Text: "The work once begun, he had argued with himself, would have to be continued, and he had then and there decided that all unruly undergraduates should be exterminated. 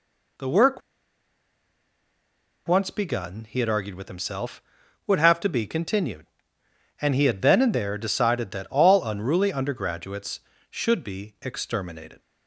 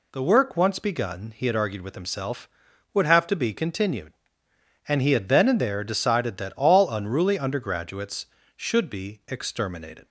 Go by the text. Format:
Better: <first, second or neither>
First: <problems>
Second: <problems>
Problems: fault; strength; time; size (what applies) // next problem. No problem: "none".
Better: second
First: pauses between "work" and "once"; strong; at 0.8 s; 1.8 s long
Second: none